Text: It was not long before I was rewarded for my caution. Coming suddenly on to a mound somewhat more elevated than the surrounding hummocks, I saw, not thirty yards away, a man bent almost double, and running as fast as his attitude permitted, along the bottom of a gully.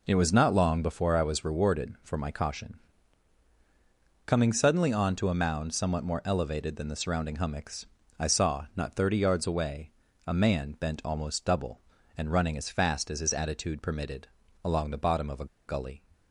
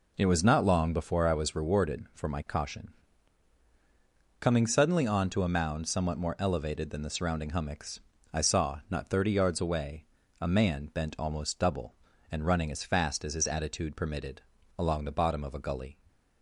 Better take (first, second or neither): second